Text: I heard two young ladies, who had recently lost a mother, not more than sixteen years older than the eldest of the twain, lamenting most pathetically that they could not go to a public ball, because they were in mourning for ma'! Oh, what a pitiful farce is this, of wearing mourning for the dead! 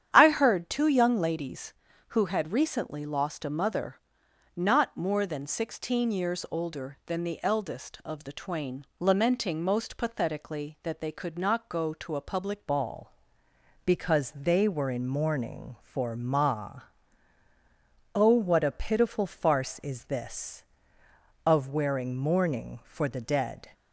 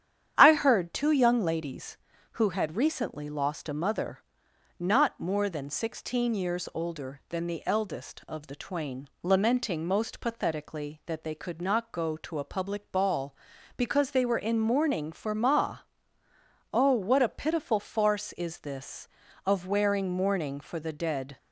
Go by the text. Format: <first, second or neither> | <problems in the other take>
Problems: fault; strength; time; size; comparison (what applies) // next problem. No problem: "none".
second | starts louder than the rest; strong; until 1.1 s; 9.5 dB; strong in the second // changes voice at "ball"; from 12.6 s on; 11.0 s long